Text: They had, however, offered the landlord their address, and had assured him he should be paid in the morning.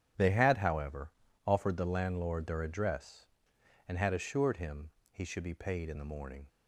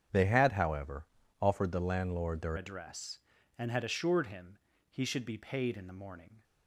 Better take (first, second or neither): first